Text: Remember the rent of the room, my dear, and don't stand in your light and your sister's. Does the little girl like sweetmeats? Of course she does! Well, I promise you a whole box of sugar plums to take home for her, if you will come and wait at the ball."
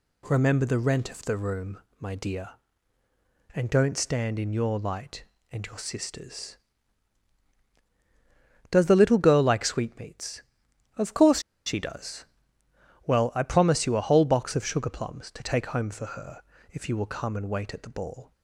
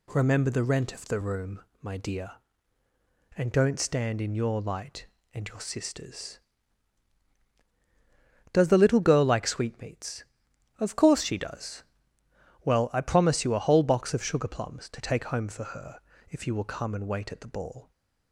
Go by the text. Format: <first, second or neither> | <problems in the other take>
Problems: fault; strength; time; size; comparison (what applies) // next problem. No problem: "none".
second | pauses between "course" and "she"; slight; at 11.4 s; 0.24 s long